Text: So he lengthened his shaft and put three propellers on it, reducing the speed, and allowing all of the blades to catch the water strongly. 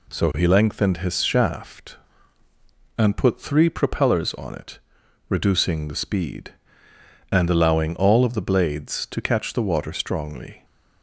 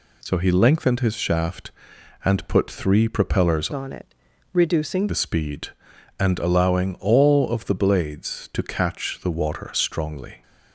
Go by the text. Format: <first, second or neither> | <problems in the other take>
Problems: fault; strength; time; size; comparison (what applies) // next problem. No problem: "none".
first | changes voice from "on" to "reducing"; from 3.7 to 5.0 s; 1.3 s long